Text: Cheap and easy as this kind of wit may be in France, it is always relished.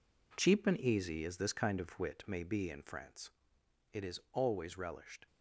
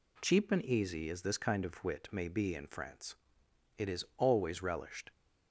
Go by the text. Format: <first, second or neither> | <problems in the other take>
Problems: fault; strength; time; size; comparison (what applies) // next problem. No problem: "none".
second | gets quieter; strong; throughout; 8.5 dB